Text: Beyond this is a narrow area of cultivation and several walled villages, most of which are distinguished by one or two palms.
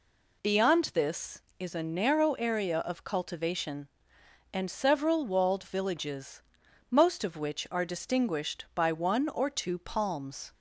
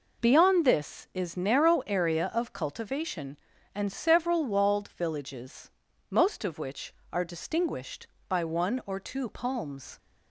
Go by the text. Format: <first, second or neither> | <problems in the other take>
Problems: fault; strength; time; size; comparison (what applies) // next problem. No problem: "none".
first | skips "a"; at 1.3 s